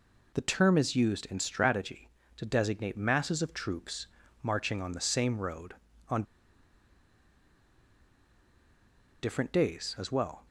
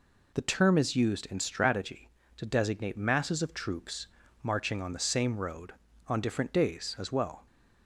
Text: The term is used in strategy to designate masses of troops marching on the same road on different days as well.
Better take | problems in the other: second | pauses between "troops" and "marching"; slight; at 4.0 s; 0.36 s long; slight in the second // pauses between "on" and "different"; strong; at 6.2 s; 3.0 s long

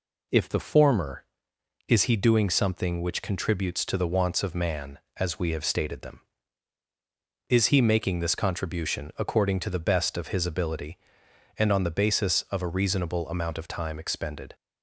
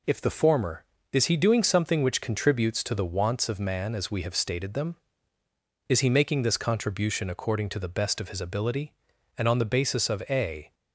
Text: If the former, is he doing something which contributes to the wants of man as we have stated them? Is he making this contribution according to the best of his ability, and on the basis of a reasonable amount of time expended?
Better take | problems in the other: first | stops before "reasonable amount of time expended"; at 10.7 s

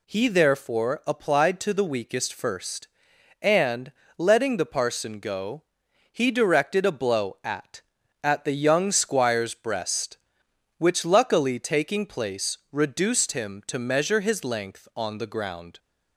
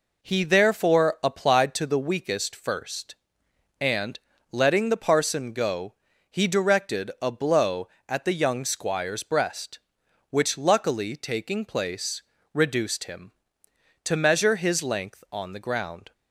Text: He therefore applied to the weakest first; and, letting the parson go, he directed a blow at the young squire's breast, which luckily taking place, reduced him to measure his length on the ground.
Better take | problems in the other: second | says "at" twice; at 8.2 s

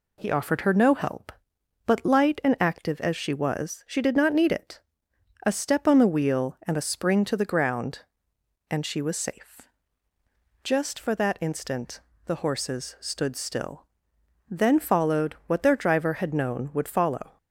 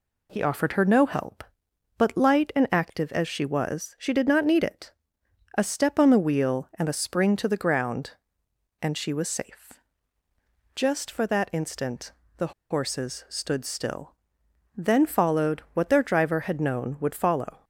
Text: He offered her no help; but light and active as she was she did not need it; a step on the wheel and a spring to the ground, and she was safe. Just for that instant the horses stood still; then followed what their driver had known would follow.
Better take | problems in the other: first | pauses between "instant" and "the"; slight; at 12.1 s; 0.24 s long; slight in the first // pauses between "the" and "horses"; slight; at 12.5 s; 0.18 s long

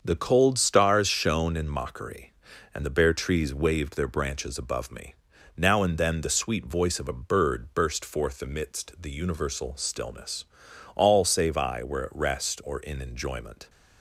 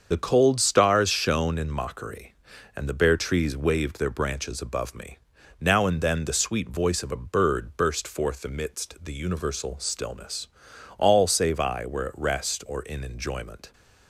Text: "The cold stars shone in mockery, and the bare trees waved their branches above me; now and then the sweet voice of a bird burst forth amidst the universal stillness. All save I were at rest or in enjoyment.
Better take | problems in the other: first | loses the start of "The"; at 0.1 s; 70 ms // starts louder than the rest; until 1.1 s; 7 dB; also in the first

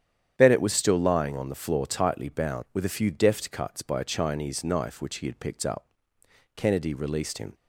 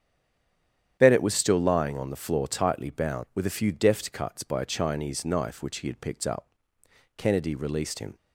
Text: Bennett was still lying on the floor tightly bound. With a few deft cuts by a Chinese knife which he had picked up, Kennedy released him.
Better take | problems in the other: first | stays silent before the first word; until 0.9 s; 0.9 s long // starts louder than the rest; strong; until 2.0 s; 9.5 dB; strong in the first

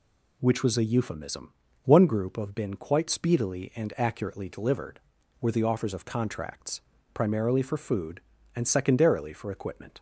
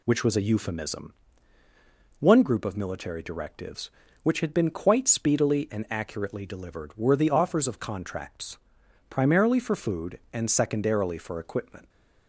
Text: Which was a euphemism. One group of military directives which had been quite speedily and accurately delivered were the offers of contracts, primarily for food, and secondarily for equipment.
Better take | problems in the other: second | skips "military directives which had"; at 2.5 s

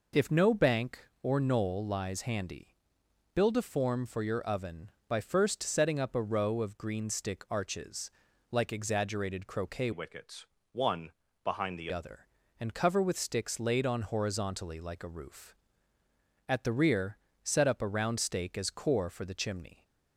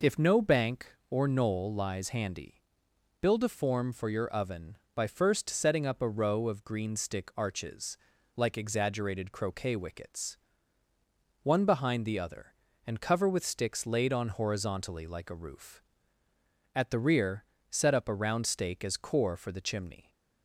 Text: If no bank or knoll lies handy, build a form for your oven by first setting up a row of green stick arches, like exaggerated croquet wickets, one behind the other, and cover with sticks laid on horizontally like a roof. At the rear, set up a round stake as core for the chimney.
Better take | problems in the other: second | changes voice from "wickets" to "the"; from 9.9 to 11.8 s; 1.9 s long // pauses between "one" and "behind"; slight; at 11.1 s; 0.32 s long

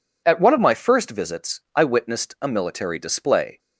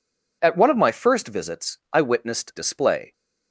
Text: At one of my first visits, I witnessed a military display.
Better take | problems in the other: first | skips "a military"; at 2.5 s

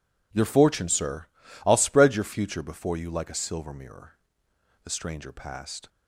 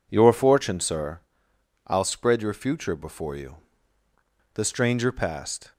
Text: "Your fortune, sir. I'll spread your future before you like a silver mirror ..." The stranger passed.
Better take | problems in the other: first | skips "like a silver mirror"; at 3.8 s

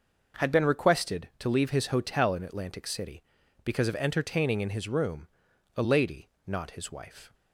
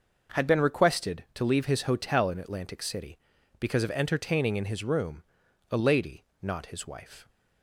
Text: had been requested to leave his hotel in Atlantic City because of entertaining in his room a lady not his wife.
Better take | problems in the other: neither | pauses between "room" and "a"; noticeable; the same in both // pauses between "lady" and "not"; slight; the same in both

